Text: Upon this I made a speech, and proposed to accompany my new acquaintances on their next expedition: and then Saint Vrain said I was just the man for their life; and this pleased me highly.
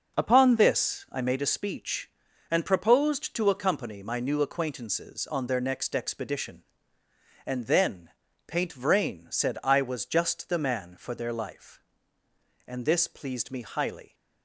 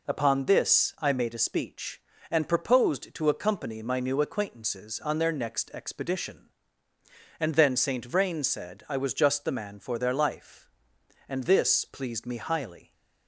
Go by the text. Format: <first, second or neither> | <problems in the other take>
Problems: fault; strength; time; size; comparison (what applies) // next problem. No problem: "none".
second | says "Paint" for "Saint"; at 8.4 s